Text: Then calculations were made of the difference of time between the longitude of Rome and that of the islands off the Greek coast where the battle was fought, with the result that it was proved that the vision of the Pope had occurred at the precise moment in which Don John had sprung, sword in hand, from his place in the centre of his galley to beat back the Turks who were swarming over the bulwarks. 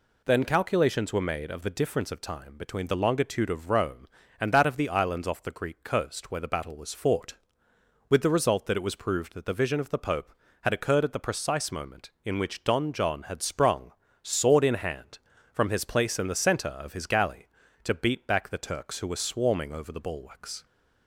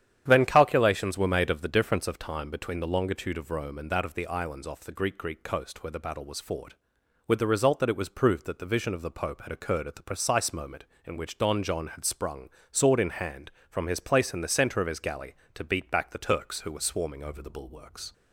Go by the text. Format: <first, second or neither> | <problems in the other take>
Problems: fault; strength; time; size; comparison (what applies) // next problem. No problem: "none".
first | starts louder than the rest; strong; until 1.2 s; 9.5 dB // says "Greek" twice; at 5.1 s